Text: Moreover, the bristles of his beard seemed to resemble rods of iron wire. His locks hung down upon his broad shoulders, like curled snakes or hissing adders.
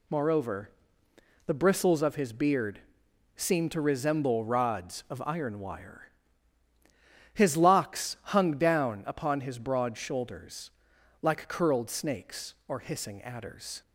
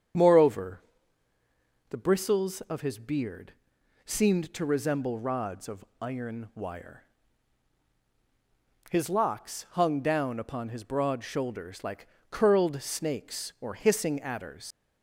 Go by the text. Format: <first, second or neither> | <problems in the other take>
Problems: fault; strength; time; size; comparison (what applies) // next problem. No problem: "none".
first | starts louder than the rest; strong; until 2.2 s; 8 dB // pauses between "beard" and "seemed"; noticeable; at 3.5 s; 0.54 s long; noticeable in the first // pauses between "of" and "iron"; slight; at 5.8 s; 0.16 s long // pauses between "like" and "curled"; slight; at 12.0 s; 0.24 s long // leaves "adders" unfinished; at 14.7 s; 75 ms